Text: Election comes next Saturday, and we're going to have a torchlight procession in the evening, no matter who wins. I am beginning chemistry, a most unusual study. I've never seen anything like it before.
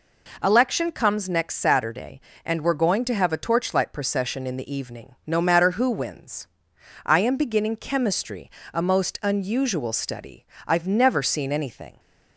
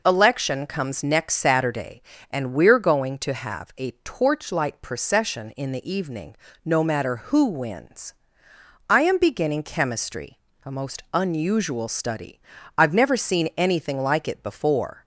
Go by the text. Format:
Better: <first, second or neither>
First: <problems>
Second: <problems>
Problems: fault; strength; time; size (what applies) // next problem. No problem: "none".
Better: second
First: stops before "like it before"; at 11.9 s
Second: none